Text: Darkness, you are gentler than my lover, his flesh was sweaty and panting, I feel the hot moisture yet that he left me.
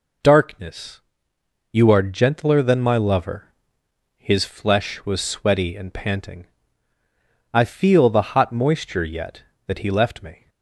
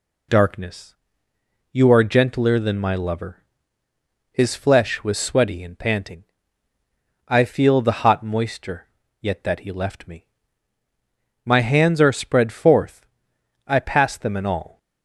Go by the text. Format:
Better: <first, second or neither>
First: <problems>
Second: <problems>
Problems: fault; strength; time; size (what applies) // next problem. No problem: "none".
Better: first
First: none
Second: pauses between "moisture" and "yet"; slight; at 8.8 s; 0.36 s long // goes on to say "My hands are spread forth I pass them in all"; strong; from 11.4 s on; 3.3 s long